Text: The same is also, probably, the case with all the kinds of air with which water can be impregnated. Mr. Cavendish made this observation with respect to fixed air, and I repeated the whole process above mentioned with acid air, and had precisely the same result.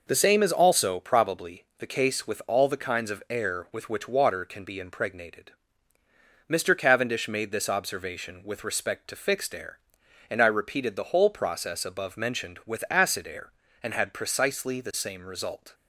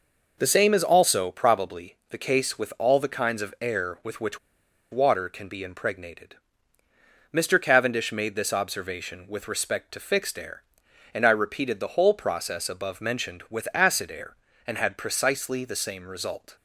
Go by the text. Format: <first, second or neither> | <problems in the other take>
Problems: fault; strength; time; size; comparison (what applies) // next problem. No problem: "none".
first | pauses between "which" and "water"; noticeable; at 4.3 s; 0.52 s long